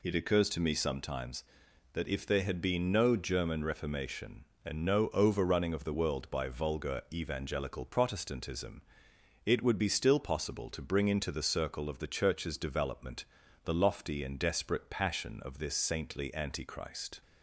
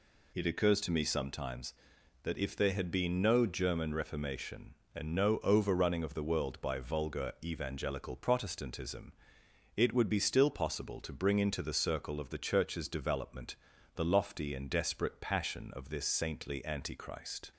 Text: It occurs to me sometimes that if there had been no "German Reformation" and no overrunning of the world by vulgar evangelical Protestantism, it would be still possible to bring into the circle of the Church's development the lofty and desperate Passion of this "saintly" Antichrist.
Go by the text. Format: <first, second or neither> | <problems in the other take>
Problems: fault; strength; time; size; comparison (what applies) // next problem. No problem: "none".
neither | pauses between "development" and "the"; the same in both